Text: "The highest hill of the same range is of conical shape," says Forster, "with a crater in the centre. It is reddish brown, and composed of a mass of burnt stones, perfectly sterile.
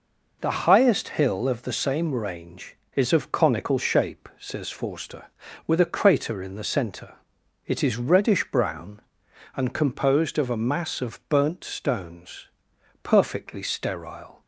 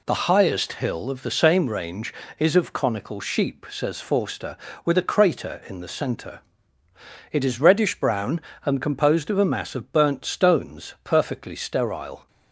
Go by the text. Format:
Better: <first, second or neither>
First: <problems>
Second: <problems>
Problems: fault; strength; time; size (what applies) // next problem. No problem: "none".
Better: first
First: none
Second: says "sheep" for "shape"; at 3.2 s